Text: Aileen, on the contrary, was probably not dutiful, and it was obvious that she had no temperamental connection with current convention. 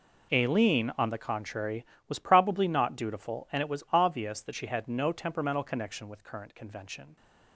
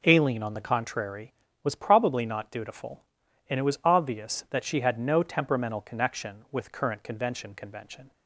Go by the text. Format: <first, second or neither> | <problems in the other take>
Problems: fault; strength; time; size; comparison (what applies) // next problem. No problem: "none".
first | says "convention" twice; at 7.5 s